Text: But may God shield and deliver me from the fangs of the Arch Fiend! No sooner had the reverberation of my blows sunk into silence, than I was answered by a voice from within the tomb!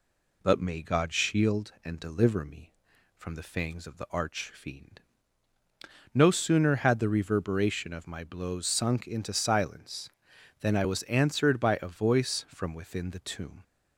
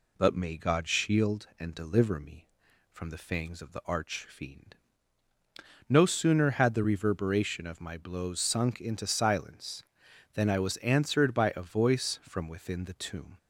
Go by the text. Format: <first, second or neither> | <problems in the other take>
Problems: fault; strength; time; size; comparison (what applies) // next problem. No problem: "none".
neither | none